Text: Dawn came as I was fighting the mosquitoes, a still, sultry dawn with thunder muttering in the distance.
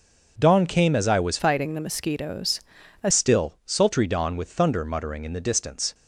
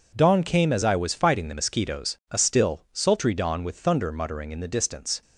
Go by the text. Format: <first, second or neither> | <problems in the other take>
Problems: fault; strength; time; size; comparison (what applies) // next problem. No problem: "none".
second | changes voice from "fighting" to "a"; from 1.3 to 3.1 s; 1.8 s long